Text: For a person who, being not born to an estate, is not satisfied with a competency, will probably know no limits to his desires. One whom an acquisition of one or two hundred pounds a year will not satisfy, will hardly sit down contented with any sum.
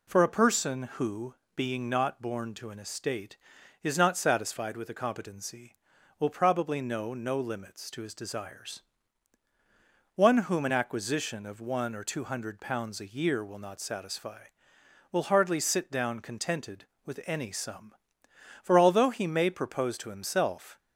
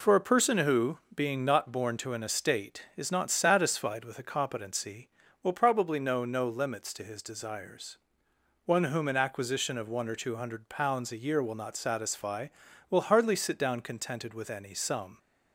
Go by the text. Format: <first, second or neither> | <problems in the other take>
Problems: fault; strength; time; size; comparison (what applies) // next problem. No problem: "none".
second | goes on to say "For although he may propose to himself"; strong; from 18.6 s on; 2.1 s long